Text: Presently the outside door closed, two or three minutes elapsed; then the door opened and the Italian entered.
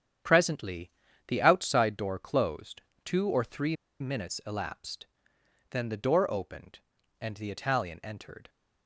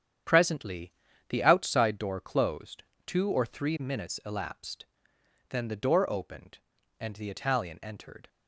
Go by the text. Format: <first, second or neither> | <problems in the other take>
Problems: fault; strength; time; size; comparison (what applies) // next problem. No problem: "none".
second | starts louder than the rest; strong; until 1.6 s; 9 dB; strong in the second // pauses between "Presently" and "the"; at 0.9 s; 0.38 s long; also in the second // pauses between "three" and "minutes"; slight; at 3.7 s; 0.25 s long